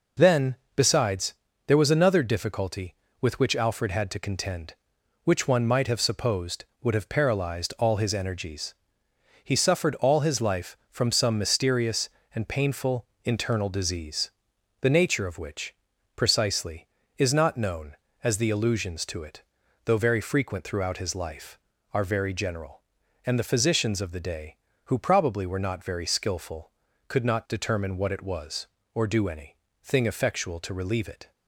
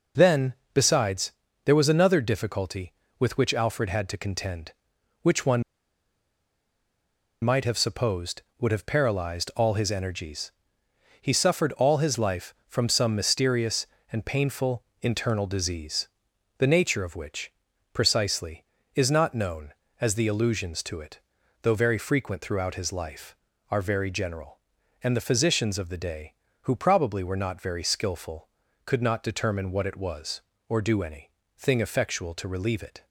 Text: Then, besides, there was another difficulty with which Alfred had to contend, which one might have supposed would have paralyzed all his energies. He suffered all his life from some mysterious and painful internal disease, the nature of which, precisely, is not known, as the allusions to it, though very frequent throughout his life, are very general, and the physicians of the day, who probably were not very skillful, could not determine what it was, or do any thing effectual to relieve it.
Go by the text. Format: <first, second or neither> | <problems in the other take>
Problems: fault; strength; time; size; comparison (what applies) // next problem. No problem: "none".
first | pauses between "one" and "might"; strong; at 5.6 s; 1.7 s long // pauses between "painful" and "internal"; slight; at 14.8 s; 0.18 s long; slight in the first // pauses between "any" and "thing"; slight; at 31.2 s; 0.28 s long; slight in the first